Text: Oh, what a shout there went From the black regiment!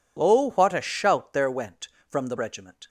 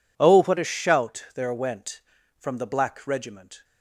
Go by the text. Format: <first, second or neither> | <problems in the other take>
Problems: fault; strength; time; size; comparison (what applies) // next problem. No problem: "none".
second | skips "black"; at 2.3 s